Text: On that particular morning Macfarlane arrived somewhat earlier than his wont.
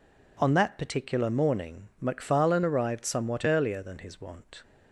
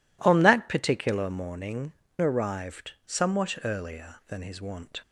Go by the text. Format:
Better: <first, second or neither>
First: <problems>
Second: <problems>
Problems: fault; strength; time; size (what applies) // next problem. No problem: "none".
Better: first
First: none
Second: skips "Macfarlane"; at 2.0 s // pauses between "arrived" and "somewhat"; slight; at 2.9 s; 0.16 s long